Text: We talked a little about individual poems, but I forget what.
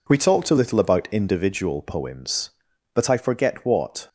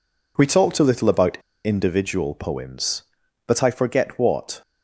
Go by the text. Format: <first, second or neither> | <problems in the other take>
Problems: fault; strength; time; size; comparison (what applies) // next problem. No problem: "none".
first | pauses between "about" and "individual"; slight; at 1.3 s; 0.26 s long